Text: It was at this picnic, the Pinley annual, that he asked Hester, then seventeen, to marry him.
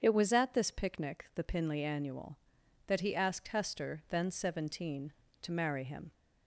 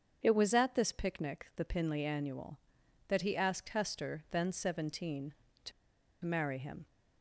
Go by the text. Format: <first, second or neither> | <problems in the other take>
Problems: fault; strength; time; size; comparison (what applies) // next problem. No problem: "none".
first | starts louder than the rest; strong; until 1.2 s; 7.5 dB; strong in the first // pauses between "to" and "marry"; noticeable; at 5.7 s; 0.52 s long